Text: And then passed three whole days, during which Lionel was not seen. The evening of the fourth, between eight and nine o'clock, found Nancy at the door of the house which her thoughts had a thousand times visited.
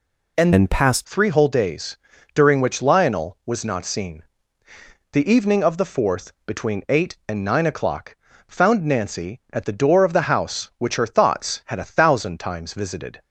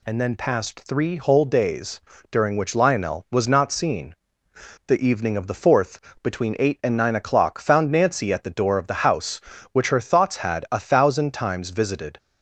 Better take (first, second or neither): second